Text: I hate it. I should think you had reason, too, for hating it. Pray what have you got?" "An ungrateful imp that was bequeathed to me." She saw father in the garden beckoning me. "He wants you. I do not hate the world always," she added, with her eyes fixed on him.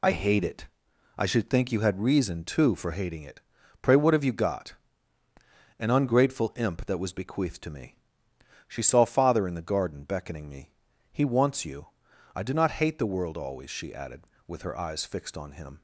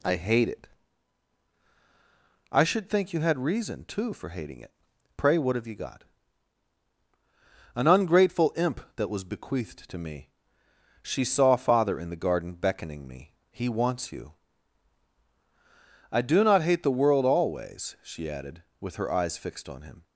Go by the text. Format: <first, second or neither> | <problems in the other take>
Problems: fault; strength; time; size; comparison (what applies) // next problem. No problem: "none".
second | loses the start of "I"; at 0.0 s; 35 ms